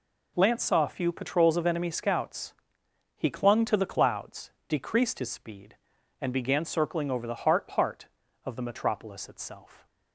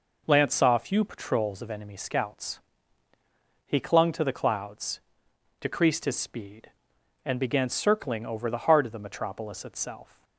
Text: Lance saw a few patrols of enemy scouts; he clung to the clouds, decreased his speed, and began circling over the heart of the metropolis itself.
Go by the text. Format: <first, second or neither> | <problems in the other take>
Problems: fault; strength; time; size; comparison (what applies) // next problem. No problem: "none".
second | says "heart" twice; at 7.7 s